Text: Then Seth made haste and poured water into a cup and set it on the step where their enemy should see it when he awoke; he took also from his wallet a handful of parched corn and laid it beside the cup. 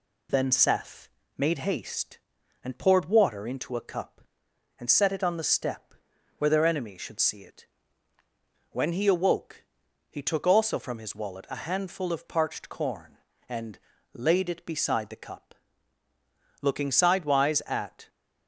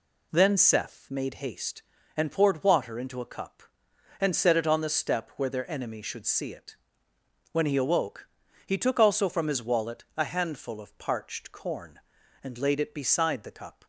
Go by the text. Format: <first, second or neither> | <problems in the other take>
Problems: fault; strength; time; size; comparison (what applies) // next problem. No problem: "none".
second | pauses between "Seth" and "made"; slight; at 1.0 s; 0.28 s long // pauses between "step" and "where"; noticeable; at 5.9 s; 0.46 s long // pauses between "it" and "when"; at 7.6 s; 1.0 s long; noticeable in the second // pauses between "and" and "laid"; slight; at 13.7 s; 0.36 s long // goes on to say "Looking sidewise at"; from 16.6 s on; 1.4 s long